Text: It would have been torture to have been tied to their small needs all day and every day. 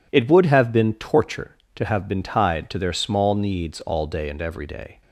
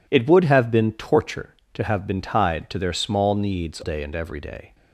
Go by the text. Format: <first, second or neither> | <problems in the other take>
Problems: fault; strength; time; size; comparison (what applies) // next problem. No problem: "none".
first | skips "all"; at 3.8 s